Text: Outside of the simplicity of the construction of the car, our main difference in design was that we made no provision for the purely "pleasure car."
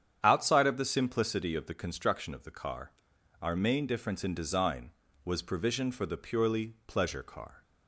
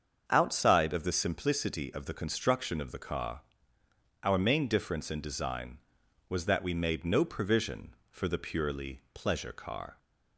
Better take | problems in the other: second | starts louder than the rest; strong; until 1.2 s; 8.5 dB; strong in the second // skips "that we made no"; at 5.4 s

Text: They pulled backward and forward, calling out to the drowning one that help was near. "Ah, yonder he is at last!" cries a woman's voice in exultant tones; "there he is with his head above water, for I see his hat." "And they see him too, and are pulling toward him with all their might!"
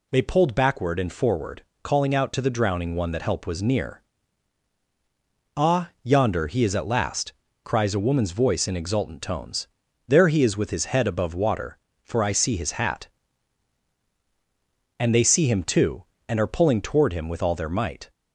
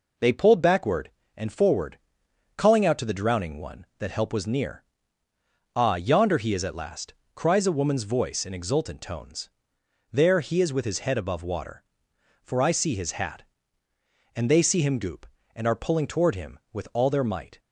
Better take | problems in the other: first | says "goop" for "too"; at 14.9 s

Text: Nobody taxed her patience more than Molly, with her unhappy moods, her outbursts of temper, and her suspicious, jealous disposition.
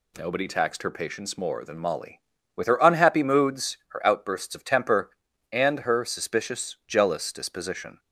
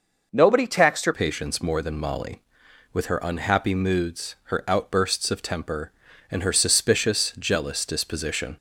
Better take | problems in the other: first | changes voice at "patience"; from 1.1 s on; 7.4 s long

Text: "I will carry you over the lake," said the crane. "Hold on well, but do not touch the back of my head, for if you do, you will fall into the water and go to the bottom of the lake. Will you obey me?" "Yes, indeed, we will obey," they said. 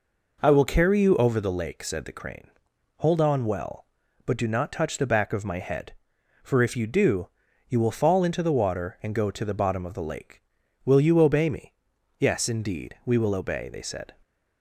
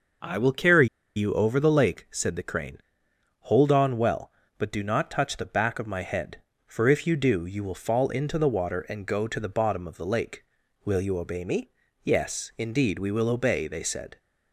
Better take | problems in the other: first | pauses between "carry" and "you"; slight; at 0.8 s; 0.27 s long

